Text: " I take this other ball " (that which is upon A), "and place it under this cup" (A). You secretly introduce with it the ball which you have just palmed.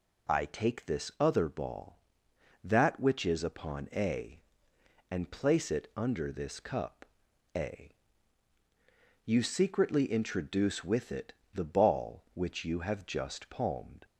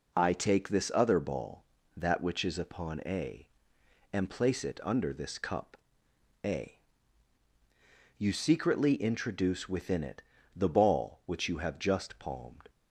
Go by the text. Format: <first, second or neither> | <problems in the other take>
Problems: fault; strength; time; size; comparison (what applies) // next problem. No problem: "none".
first | says "within" for "with"; at 9.6 s // pauses between "it" and "the"; slight; at 10.2 s; 0.34 s long; slight in the first